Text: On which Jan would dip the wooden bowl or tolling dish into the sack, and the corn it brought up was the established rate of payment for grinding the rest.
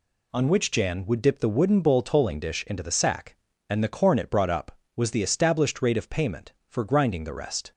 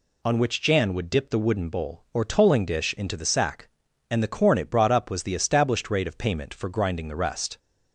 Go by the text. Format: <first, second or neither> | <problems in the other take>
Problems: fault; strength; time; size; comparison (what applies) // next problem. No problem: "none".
second | skips "or"; at 2.0 s